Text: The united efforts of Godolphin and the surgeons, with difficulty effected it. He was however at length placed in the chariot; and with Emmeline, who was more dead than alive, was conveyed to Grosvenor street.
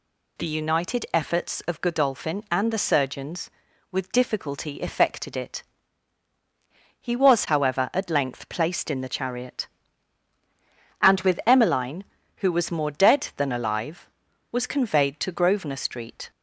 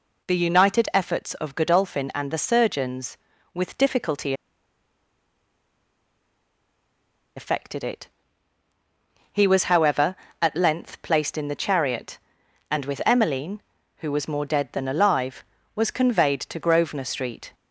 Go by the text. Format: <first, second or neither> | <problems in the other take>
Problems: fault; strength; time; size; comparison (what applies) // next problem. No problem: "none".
first | pauses between "difficulty" and "effected"; strong; at 4.3 s; 3.0 s long